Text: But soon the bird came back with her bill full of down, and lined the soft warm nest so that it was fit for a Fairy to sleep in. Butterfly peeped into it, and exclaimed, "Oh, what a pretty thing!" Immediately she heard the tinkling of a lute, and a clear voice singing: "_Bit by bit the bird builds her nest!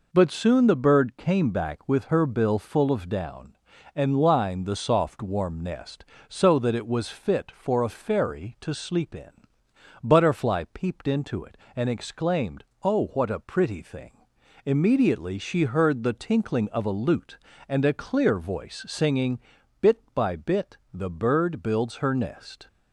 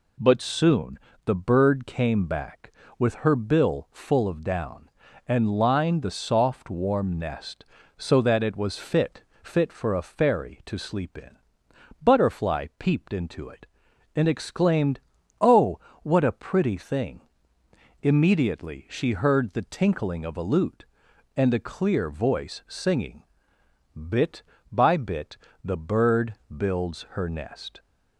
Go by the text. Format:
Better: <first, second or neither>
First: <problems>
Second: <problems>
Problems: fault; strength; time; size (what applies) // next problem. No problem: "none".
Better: first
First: pauses between "bit" and "the"; slight; at 20.7 s; 0.18 s long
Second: pauses between "soon" and "the"; slight; at 0.9 s; 0.26 s long // says "fit" twice; at 9.4 s // pauses between "bit" and "the"; slight; at 25.3 s; 0.26 s long // pauses between "bird" and "builds"; slight; at 26.3 s; 0.16 s long